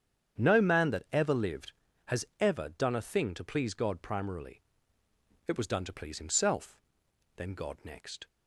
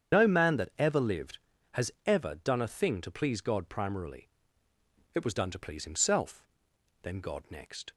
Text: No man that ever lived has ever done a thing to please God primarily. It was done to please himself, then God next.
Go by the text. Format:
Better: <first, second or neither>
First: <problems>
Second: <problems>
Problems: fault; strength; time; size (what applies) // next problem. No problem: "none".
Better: first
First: starts louder than the rest; strong; until 1.4 s; 8.5 dB // pauses between "has" and "ever"; slight; at 2.2 s; 0.16 s long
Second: loses the start of "No"; at 0.1 s; 85 ms // starts louder than the rest; strong; until 1.2 s; 8 dB // pauses between "has" and "ever"; slight; at 1.8 s; 0.16 s long